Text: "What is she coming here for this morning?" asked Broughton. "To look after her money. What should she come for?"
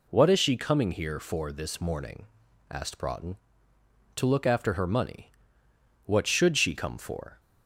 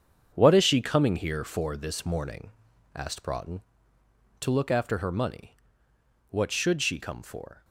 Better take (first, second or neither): first